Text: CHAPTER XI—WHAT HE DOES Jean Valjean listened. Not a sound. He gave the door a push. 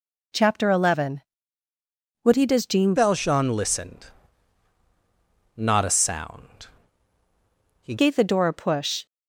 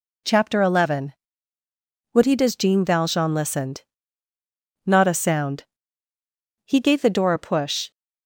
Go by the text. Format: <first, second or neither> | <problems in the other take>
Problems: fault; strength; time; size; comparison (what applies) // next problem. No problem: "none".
second | changes voice from "Valjean" to "He"; from 2.9 to 7.9 s; 5.0 s long